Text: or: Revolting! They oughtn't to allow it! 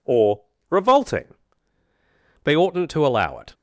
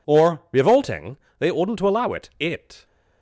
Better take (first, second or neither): first